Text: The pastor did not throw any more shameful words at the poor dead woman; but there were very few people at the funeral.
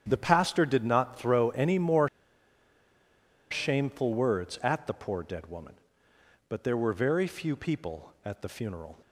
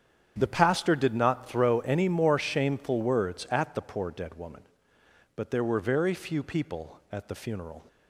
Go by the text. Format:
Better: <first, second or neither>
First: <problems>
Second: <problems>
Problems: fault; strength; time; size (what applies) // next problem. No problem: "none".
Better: second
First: starts louder than the rest; strong; until 1.0 s; 8.5 dB // pauses between "more" and "shameful"; strong; at 2.0 s; 1.4 s long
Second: starts louder than the rest; strong; until 1.3 s; 8.5 dB